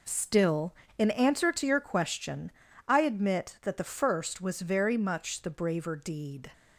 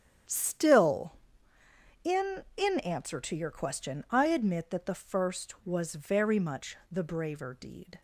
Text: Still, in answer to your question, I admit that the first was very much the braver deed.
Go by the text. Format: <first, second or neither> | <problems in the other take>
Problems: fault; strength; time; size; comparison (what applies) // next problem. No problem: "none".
first | starts louder than the rest; strong; until 2.1 s; 9 dB // says "in" twice; at 2.5 s